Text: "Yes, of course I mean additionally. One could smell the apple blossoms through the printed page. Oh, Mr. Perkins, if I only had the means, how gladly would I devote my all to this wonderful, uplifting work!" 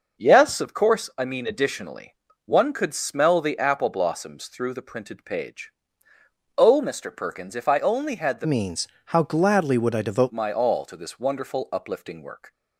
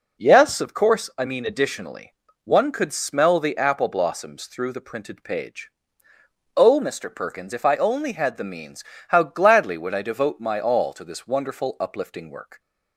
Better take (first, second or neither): second